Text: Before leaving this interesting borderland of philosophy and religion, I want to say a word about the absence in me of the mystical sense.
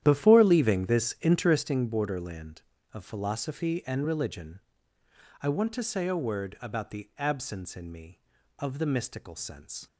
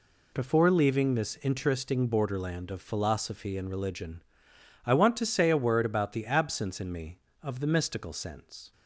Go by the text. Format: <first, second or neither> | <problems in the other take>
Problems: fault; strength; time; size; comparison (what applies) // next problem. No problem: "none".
second | starts louder than the rest; strong; until 1.7 s; 11 dB